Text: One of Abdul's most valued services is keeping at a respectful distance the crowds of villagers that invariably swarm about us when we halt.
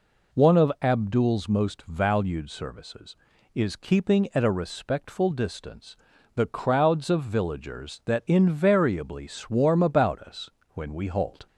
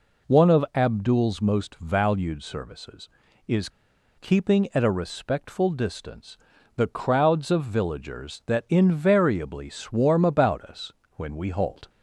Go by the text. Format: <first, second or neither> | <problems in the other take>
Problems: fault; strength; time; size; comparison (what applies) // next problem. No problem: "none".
first | pauses between "is" and "keeping"; noticeable; at 3.6 s; 0.49 s long // pauses between "distance" and "the"; at 6.3 s; 0.40 s long; also in the first // pauses between "us" and "when"; slight; at 10.9 s; 0.24 s long; slight in the first